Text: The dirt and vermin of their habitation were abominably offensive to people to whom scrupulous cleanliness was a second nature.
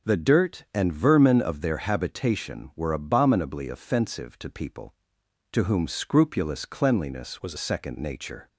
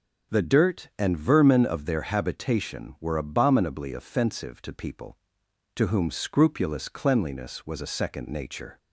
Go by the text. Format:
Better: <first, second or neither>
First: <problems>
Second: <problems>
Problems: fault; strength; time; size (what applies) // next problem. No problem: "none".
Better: second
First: starts louder than the rest; until 1.1 s; 6.5 dB // changes voice from "was" to "a"; from 7.4 to 7.5 s; 0.1 s long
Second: starts louder than the rest; until 1.4 s; 7 dB